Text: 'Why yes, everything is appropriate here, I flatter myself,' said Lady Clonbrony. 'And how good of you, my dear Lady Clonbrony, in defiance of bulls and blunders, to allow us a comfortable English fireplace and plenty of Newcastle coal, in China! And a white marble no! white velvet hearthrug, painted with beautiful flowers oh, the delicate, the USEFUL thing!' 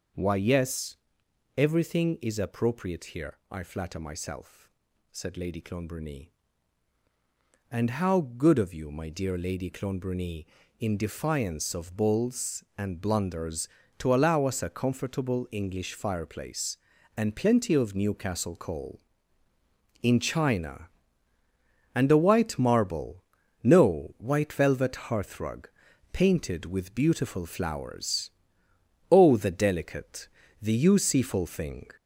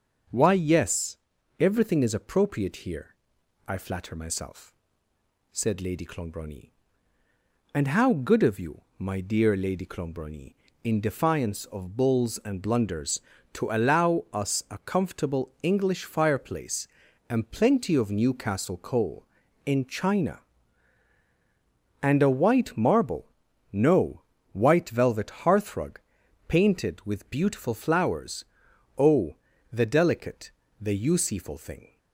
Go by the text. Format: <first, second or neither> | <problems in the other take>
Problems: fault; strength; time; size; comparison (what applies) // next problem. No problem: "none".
second | gets louder; throughout; 3.5 dB // starts louder than the rest; noticeable; until 1.7 s; 6 dB; also in the second // pauses between "marble" and "no"; at 23.2 s; 0.42 s long; also in the second // pauses between "flowers" and "oh"; noticeable; at 28.2 s; 0.80 s long; noticeable in the second